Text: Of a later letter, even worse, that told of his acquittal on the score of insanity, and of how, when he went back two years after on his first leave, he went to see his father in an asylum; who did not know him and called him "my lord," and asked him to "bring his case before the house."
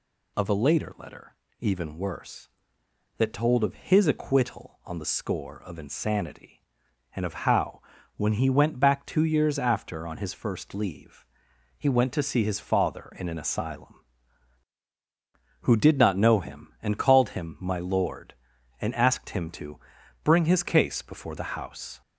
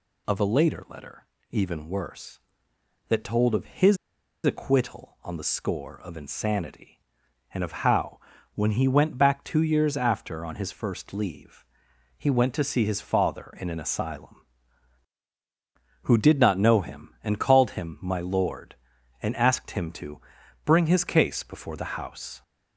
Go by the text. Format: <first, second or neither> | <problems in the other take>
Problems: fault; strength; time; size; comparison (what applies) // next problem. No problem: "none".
first | pauses between "his" and "acquittal"; noticeable; at 3.9 s; 0.47 s long // pauses between "to" and "bring"; noticeable; at 20.2 s; 0.46 s long; noticeable in the first